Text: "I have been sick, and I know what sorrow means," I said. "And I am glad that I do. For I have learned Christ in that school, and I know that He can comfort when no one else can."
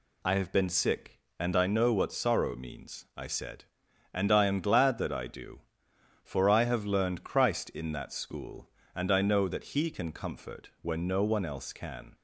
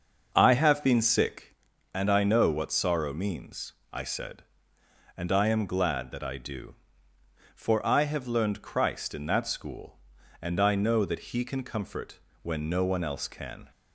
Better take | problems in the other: first | starts louder than the rest; until 1.6 s; 6.5 dB // pauses between "comfort" and "when"; slight; at 12.2 s; 0.22 s long

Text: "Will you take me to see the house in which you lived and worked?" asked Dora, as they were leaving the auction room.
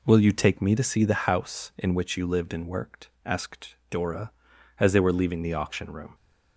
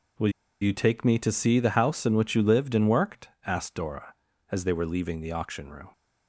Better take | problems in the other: first | pauses between "Will" and "you"; slight; at 0.3 s; 0.30 s long

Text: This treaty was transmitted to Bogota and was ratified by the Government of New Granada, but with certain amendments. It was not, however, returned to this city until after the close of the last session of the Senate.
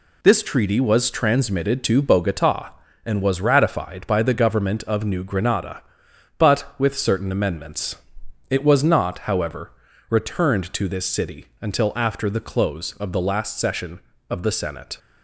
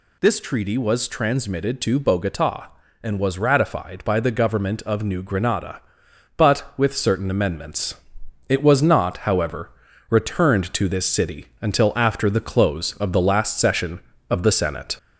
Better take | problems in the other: first | gets louder; slight; throughout; 2 dB

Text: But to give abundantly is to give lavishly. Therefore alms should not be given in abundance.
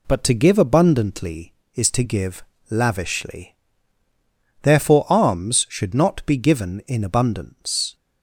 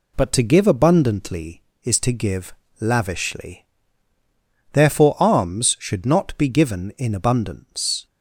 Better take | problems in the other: neither | pauses between "give" and "lavishly"; slight; the same in both

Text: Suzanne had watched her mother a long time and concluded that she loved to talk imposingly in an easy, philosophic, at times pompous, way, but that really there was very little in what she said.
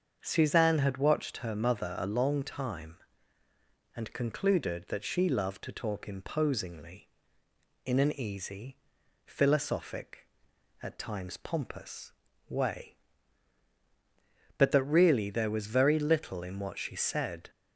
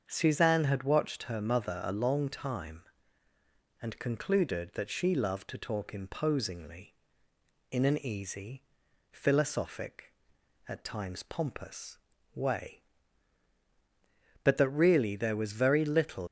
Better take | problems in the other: first | starts louder than the rest; until 1.0 s; 7 dB; also in the first // stops before "in what she said"; at 16.2 s

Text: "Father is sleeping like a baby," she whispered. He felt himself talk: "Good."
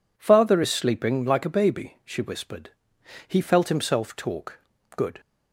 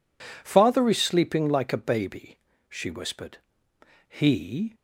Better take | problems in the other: first | stops before "felt himself talk Good"; at 4.7 s

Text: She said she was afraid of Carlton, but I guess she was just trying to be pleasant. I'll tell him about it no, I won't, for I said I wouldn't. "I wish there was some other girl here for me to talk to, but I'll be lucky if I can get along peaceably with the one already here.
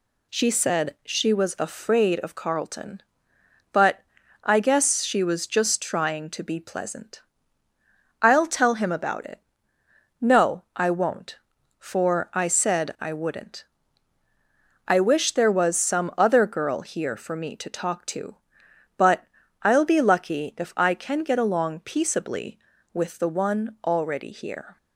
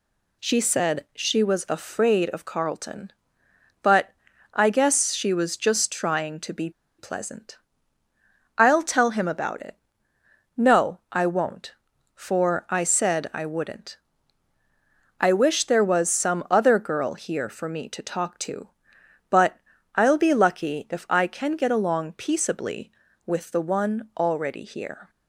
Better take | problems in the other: first | pauses between "but" and "I"; at 4.1 s; 0.42 s long; also in the first // pauses between "be" and "pleasant"; slight; at 6.6 s; 0.28 s long // pauses between "it" and "no"; noticeable; at 9.7 s; 0.82 s long; noticeable in the first // pauses between "but" and "I'll"; slight; at 19.5 s; 0.36 s long; slight in the first

